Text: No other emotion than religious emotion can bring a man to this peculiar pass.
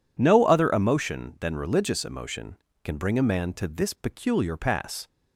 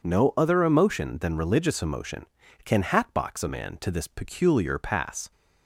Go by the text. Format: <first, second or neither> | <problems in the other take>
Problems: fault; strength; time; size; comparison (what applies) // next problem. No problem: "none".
first | says "hatbox" for "bring"; at 2.8 s